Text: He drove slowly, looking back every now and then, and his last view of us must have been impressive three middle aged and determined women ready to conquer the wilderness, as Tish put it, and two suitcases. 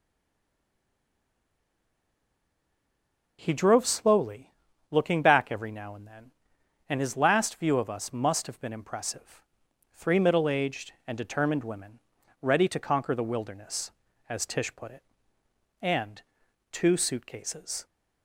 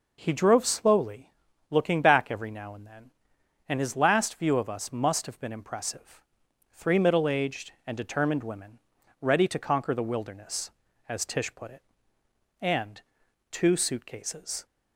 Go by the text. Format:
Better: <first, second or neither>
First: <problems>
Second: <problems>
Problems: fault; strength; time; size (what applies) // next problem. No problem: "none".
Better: second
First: stays silent before the first word; strong; until 3.3 s; 3.3 s long // pauses between "impressive" and "three"; noticeable; at 9.4 s; 0.50 s long // pauses between "women" and "ready"; at 11.9 s; 0.42 s long // pauses between "and" and "two"; noticeable; at 16.1 s; 0.50 s long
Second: pauses between "impressive" and "three"; noticeable; at 6.2 s; 0.50 s long // pauses between "women" and "ready"; at 8.7 s; 0.42 s long // pauses between "and" and "two"; noticeable; at 12.9 s; 0.50 s long